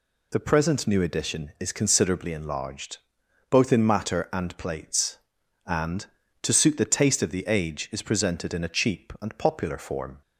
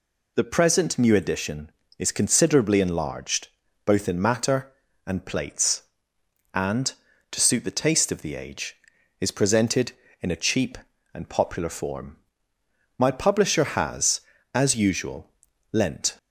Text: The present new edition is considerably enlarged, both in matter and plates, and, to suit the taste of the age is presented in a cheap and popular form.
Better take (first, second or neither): first